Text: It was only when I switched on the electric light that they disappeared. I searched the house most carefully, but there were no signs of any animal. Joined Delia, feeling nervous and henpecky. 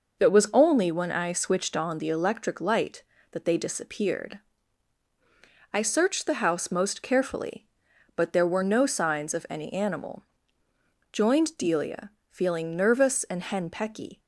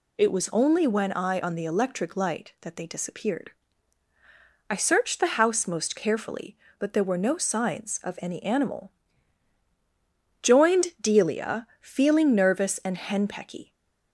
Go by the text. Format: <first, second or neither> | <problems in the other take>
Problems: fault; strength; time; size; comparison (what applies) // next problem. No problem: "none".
first | skips "switched"; at 1.4 s // stays silent after the last word; slight; from 13.6 s on; 0.5 s long